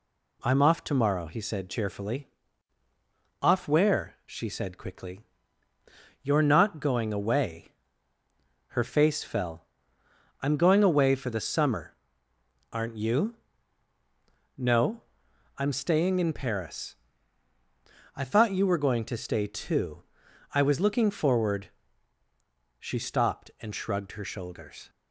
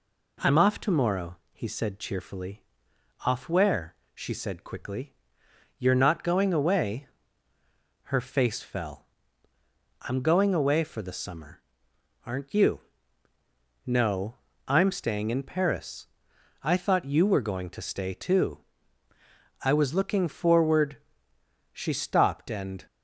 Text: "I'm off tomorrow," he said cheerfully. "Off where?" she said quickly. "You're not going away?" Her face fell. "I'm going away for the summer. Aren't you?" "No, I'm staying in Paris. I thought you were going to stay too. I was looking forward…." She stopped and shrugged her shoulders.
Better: first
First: none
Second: stops before "shrugged her shoulders"; at 22.8 s

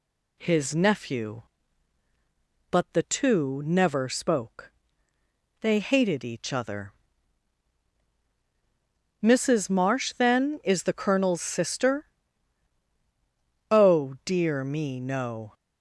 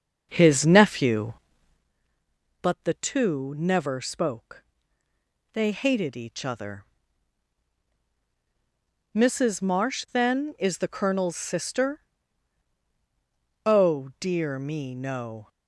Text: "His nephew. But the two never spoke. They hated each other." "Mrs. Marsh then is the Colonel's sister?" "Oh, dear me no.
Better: first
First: none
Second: starts louder than the rest; until 1.9 s; 6.5 dB

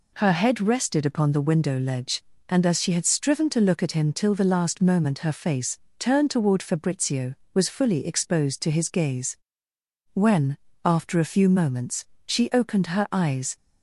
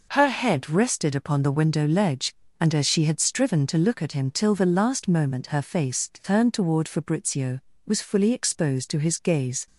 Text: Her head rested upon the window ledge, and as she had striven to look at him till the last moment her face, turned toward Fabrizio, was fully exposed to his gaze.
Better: second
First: goes on to say "When after a few moments she opened her eyes"; strong; from 10.1 s on; 3.4 s long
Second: none

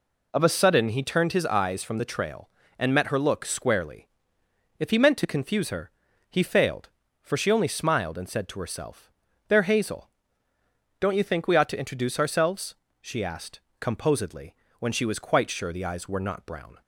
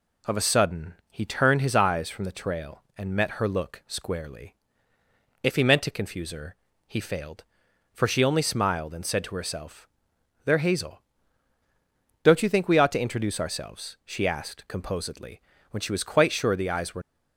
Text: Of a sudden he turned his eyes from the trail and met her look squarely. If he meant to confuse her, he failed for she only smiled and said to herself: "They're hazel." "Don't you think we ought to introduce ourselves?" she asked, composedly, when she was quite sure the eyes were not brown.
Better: first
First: none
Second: pauses between "sudden" and "he"; slight; at 0.9 s; 0.16 s long // stops before "not brown"; at 17.0 s

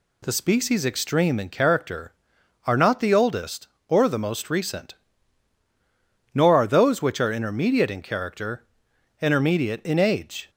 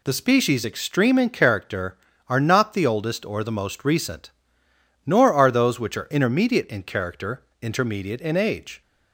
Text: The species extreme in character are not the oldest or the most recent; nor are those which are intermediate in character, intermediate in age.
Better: neither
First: none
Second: none

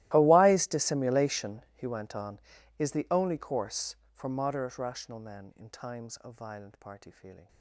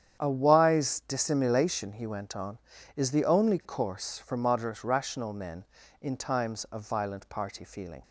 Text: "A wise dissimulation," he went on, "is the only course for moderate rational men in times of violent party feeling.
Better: second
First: gets quieter; strong; throughout; 23.5 dB // starts louder than the rest; strong; until 1.1 s; 16.5 dB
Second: starts louder than the rest; strong; until 1.2 s; 9 dB

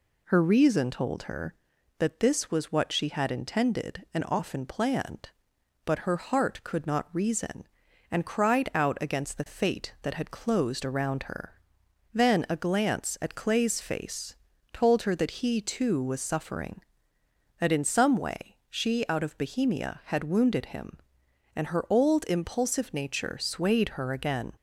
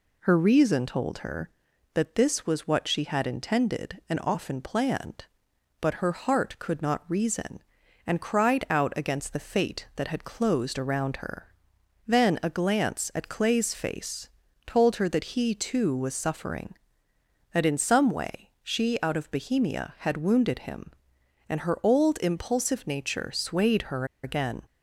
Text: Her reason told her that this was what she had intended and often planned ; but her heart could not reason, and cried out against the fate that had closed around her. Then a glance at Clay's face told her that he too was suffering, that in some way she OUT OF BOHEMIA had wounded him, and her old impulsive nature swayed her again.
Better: first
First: pauses between "face" and "told"; at 14.3 s; 0.38 s long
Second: pauses between "face" and "told"; at 14.2 s; 0.38 s long // pauses between "her" and "again"; slight; at 24.0 s; 0.18 s long

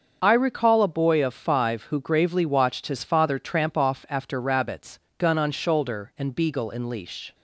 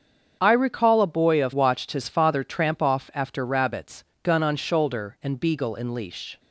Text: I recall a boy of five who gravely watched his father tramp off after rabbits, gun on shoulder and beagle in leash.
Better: first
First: starts louder than the rest; until 1.2 s; 7 dB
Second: starts louder than the rest; strong; until 1.4 s; 7.5 dB // skips "five who gravely"; at 1.5 s

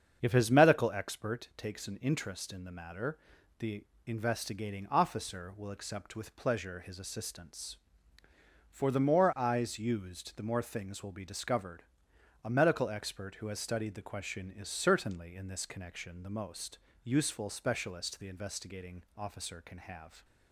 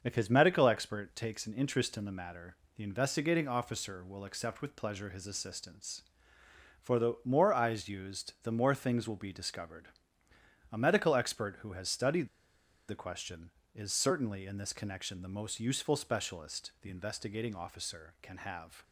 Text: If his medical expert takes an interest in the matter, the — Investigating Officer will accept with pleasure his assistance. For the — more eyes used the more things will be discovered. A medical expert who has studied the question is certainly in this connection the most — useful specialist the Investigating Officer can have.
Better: first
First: starts louder than the rest; strong; until 1.2 s; 7.5 dB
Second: starts louder than the rest; until 1.0 s; 6.5 dB // pauses between "studied" and "the"; noticeable; at 12.2 s; 0.60 s long

